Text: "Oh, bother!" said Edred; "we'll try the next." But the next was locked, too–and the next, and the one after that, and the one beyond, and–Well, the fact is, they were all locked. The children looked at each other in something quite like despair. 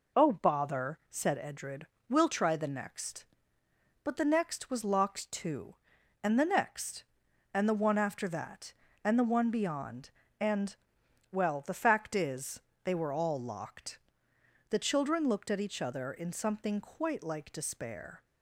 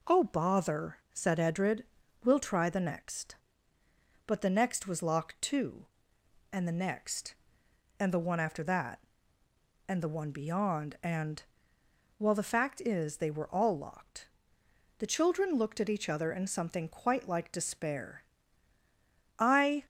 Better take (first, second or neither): first